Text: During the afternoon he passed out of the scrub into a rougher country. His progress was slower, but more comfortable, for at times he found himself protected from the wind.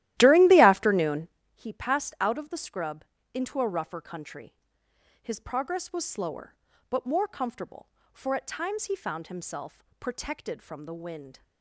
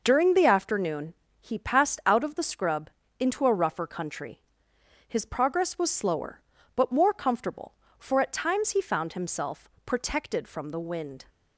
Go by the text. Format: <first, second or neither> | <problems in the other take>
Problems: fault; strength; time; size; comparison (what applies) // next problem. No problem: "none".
second | starts louder than the rest; strong; until 1.4 s; 14.5 dB // pauses between "afternoon" and "he"; slight; at 1.2 s; 0.26 s long; slight in the second // pauses between "scrub" and "into"; slight; at 3.0 s; 0.30 s long; slight in the second // pauses between "himself" and "protected"; slight; at 9.8 s; 0.16 s long; slight in the second